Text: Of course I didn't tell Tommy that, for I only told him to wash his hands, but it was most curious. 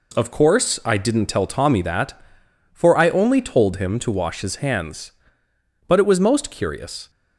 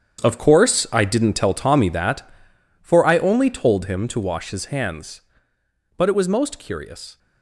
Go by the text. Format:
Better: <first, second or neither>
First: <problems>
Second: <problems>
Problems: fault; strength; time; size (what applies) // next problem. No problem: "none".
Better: first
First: none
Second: gets quieter; strong; throughout; 12.5 dB